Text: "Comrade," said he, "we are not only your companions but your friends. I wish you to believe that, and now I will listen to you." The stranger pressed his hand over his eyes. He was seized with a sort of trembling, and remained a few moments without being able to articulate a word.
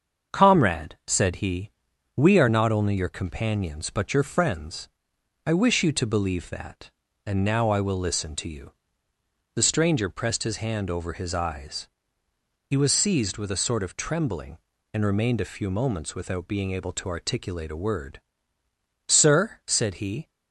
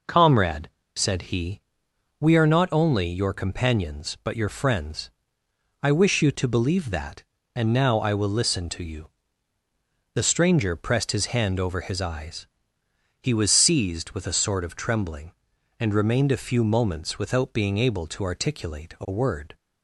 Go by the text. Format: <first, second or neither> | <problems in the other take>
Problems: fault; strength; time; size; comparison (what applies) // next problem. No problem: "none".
second | starts louder than the rest; until 1.4 s; 7 dB // goes on to say "Sir said he"; noticeable; from 19.0 s on; 1.2 s long